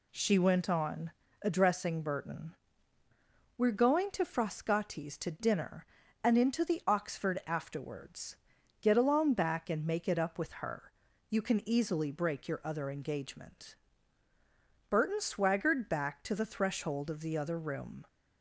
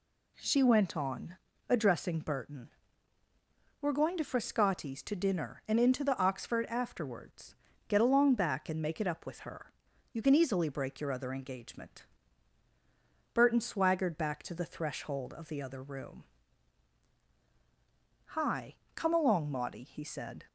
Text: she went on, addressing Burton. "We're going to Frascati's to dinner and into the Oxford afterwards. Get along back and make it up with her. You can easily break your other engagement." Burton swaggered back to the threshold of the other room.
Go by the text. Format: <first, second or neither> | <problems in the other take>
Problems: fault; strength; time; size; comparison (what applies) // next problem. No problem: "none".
first | goes on to say "Hi Come along Maudie he said"; strong; from 18.2 s on; 2.1 s long